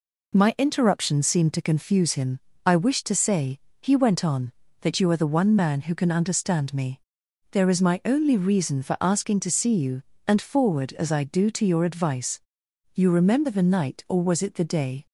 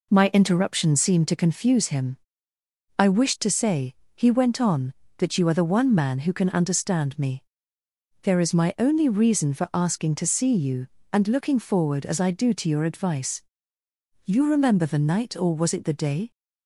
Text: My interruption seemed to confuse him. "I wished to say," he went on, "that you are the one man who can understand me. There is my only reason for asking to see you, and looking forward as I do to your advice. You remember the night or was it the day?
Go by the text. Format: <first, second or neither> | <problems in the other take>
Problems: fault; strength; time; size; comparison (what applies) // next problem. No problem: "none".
second | skips "looking"; at 10.4 s